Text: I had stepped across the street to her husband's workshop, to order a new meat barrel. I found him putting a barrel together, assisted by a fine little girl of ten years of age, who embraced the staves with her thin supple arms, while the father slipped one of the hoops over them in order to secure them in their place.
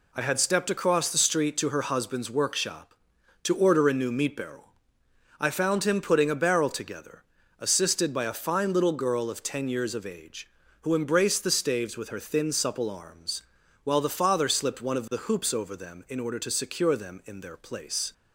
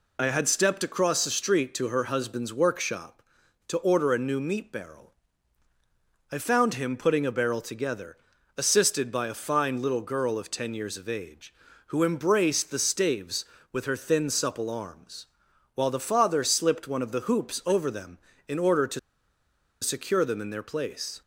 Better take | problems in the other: first | pauses between "to" and "secure"; noticeable; at 18.9 s; 0.83 s long

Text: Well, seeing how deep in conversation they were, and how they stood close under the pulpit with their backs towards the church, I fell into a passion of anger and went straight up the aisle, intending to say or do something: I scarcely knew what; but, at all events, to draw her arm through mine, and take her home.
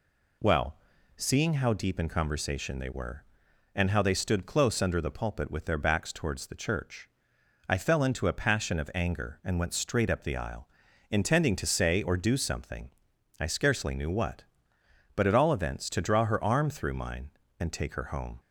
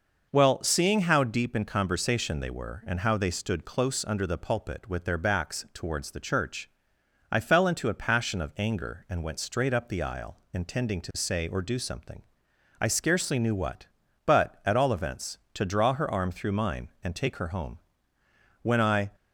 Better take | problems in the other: first | goes on to say "When I"; slight; from 18.6 s on; 0.48 s long

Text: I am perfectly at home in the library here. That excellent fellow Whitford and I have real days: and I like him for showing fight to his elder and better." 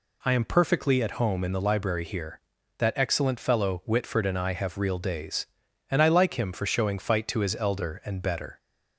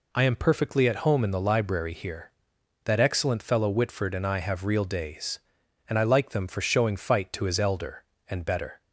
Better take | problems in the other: first | says "them" for "him"; at 6.3 s

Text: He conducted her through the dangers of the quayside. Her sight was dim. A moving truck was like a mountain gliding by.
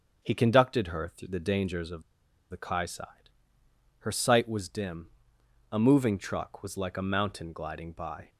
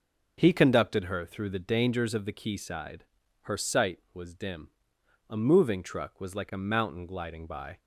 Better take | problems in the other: second | starts louder than the rest; until 1.2 s; 6.5 dB // pauses between "of" and "the"; noticeable; at 2.0 s; 0.49 s long

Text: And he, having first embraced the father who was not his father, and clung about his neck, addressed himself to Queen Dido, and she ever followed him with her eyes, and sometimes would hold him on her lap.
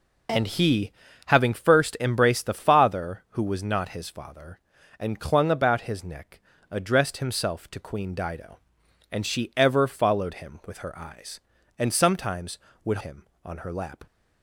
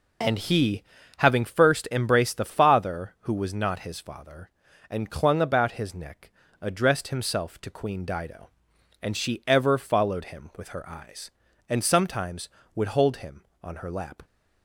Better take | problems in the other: second | skips "hold"; at 12.9 s

